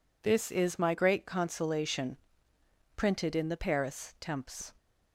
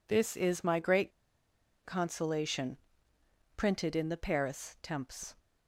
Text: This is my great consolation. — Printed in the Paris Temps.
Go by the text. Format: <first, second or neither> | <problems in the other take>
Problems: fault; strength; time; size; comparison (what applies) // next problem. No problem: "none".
first | pauses between "great" and "consolation"; noticeable; at 1.1 s; 0.74 s long